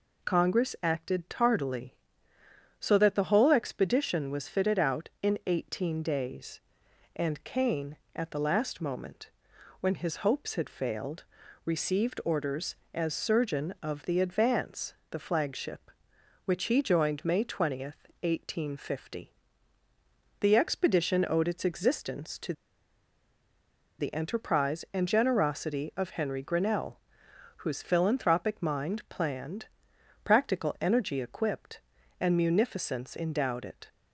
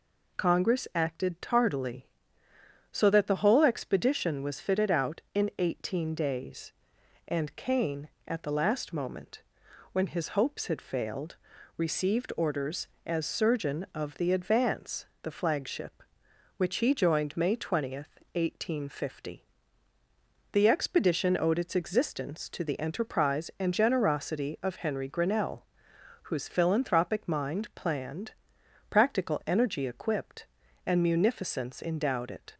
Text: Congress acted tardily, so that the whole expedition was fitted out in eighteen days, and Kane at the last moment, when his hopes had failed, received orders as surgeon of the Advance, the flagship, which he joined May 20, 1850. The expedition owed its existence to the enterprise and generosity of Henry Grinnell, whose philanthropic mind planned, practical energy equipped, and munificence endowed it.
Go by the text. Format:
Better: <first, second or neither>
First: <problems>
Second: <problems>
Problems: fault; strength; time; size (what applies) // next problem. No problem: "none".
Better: second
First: pauses between "to" and "the"; strong; at 22.5 s; 1.4 s long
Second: none